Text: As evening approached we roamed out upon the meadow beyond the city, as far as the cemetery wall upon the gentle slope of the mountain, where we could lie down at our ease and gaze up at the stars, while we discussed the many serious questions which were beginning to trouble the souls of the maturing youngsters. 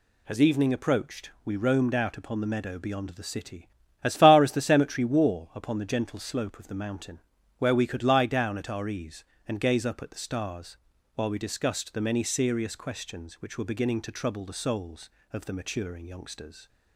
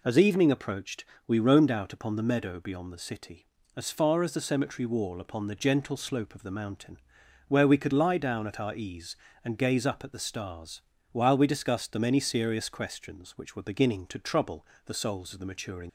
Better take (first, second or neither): first